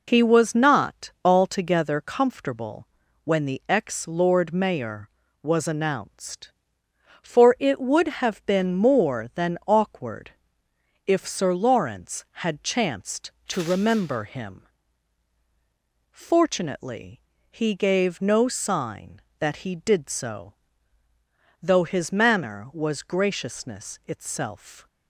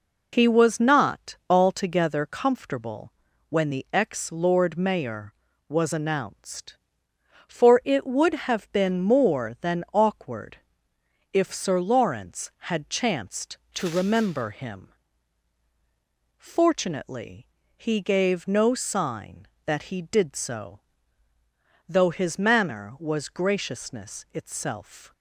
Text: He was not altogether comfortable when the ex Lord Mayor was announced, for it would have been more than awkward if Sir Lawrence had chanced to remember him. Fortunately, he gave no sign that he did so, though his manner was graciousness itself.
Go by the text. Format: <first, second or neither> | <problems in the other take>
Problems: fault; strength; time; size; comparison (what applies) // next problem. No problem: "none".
neither | pauses between "comfortable" and "when"; the same in both // pauses between "awkward" and "if"; noticeable; the same in both